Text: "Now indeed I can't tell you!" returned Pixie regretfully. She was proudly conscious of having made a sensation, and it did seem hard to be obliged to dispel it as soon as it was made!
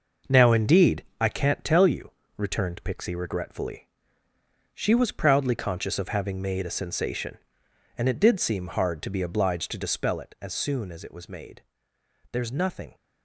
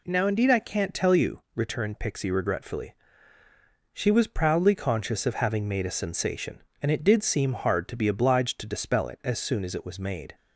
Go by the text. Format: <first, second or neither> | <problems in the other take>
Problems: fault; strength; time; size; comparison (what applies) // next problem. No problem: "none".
second | pauses between "indeed" and "I"; slight; at 1.0 s; 0.16 s long // goes on to say "There's nothing"; noticeable; from 12.3 s on; 0.64 s long